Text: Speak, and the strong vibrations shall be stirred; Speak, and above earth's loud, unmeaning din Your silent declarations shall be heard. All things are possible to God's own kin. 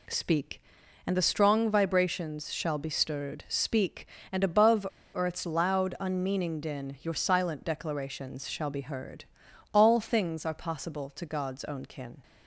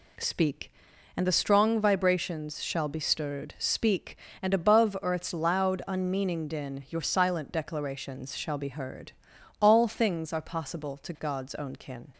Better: second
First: pauses between "above" and "earth's"; slight; at 4.8 s; 0.28 s long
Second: none

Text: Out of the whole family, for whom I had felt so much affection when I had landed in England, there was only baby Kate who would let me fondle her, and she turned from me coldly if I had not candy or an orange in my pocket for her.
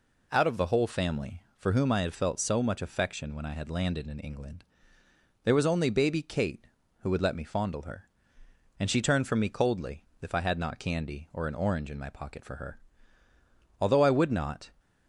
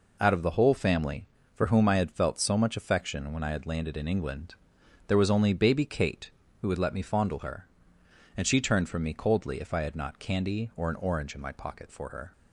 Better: second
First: pauses between "coldly" and "if"; slight; at 10.0 s; 0.18 s long // goes on to say "Although I would not"; noticeable; from 13.7 s on; 0.92 s long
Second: none

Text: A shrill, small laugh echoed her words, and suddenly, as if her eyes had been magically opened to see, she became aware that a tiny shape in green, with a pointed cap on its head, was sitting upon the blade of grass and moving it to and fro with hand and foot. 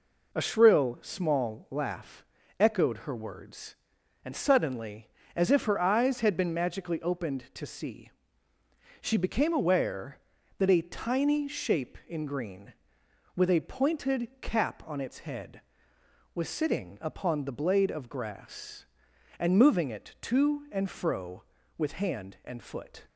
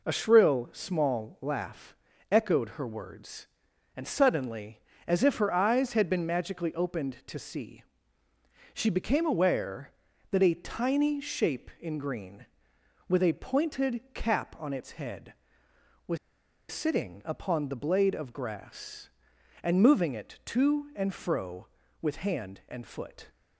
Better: first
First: pauses between "laugh" and "echoed"; slight; at 2.2 s; 0.33 s long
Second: pauses between "laugh" and "echoed"; slight; at 1.9 s; 0.34 s long // pauses between "was" and "sitting"; noticeable; at 16.1 s; 0.53 s long

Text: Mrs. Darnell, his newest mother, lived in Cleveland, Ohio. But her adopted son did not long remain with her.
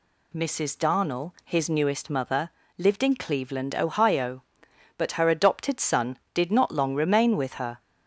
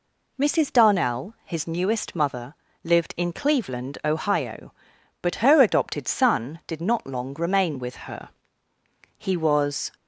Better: first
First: none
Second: goes on to say "He was"; noticeable; from 9.1 s on; 0.74 s long

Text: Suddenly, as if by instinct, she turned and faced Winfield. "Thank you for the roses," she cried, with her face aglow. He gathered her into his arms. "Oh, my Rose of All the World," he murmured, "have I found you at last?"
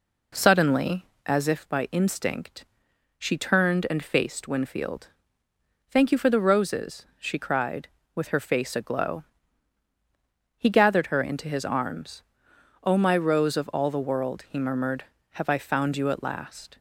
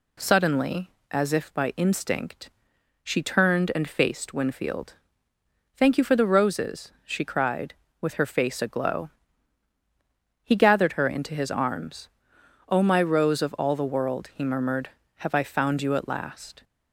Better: second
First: starts louder than the rest; until 1.5 s; 3.5 dB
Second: none

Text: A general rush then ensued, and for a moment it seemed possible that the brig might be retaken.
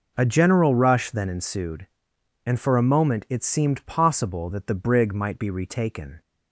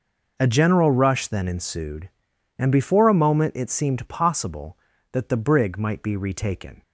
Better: first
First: none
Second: says "before" for "for"; at 2.6 s

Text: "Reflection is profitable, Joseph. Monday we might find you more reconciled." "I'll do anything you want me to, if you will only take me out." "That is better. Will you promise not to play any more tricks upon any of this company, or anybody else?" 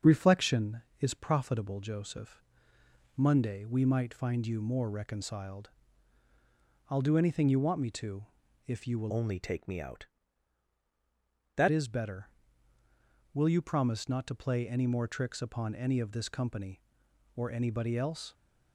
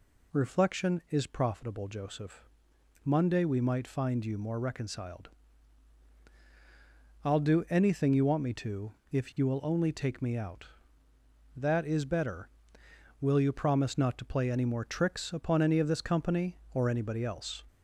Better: second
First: starts louder than the rest; until 1.2 s; 7 dB // changes voice from "only" to "That"; from 9.0 to 11.6 s; 2.6 s long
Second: none

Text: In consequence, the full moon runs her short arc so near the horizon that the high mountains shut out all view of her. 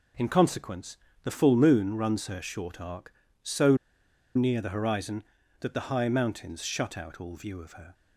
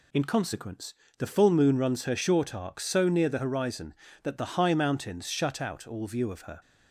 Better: second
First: pauses between "so" and "near"; noticeable; at 3.7 s; 0.59 s long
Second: none

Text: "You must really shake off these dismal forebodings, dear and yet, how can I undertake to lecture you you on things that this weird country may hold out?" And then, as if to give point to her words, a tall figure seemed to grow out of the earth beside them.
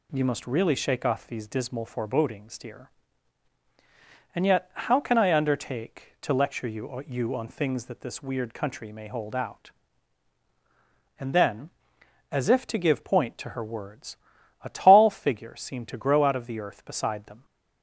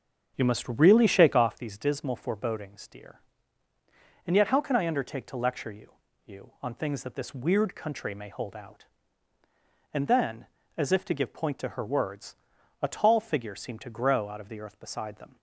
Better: first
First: none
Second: starts louder than the rest; until 1.5 s; 7 dB // pauses between "you" and "you"; slight; at 5.9 s; 0.30 s long

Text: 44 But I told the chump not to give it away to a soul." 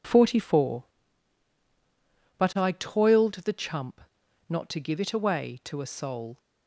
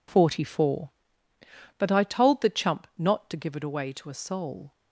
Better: second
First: says "toiled" for "told"; at 2.7 s // pauses between "chump" and "not"; noticeable; at 3.9 s; 0.48 s long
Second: none

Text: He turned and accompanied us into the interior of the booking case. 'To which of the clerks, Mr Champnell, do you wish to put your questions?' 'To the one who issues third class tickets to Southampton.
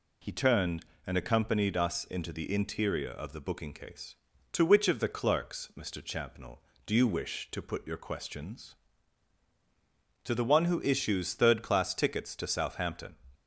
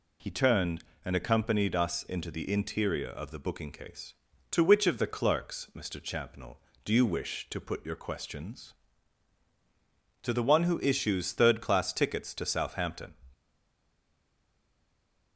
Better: first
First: none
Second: stays silent after the last word; noticeable; from 13.3 s on; 2.0 s long

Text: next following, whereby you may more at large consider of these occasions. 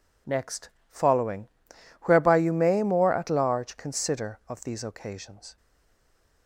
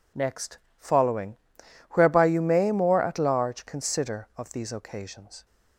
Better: second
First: pauses between "next" and "following"; slight; at 0.6 s; 0.22 s long // stays silent after the last word; slight; from 5.5 s on; 0.9 s long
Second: pauses between "next" and "following"; slight; at 0.5 s; 0.22 s long

